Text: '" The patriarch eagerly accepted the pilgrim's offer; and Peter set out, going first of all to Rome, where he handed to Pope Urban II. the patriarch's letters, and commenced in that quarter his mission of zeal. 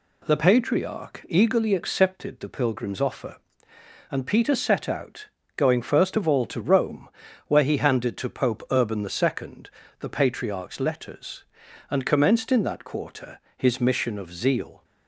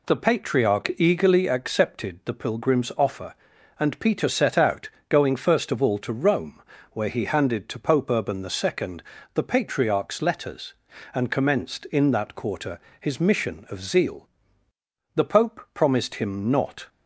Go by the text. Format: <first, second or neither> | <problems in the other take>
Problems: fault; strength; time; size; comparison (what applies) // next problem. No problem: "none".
first | pauses between "quarter" and "his"; slight; at 12.8 s; 0.20 s long; slight in the first // goes on to say "The pope promised him not"; strong; from 15.1 s on; 1.7 s long